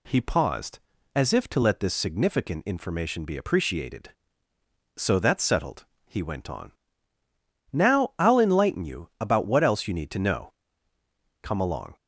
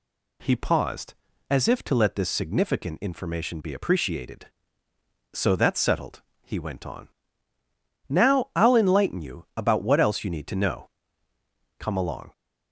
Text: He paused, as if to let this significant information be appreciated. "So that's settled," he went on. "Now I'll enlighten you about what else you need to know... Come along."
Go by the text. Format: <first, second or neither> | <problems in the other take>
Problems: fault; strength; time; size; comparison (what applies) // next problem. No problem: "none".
neither | none